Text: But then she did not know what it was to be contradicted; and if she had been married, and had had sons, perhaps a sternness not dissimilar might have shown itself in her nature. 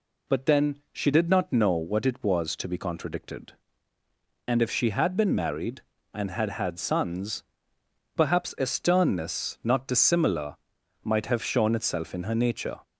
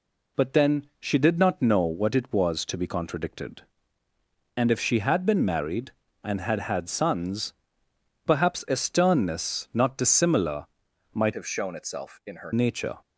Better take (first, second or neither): first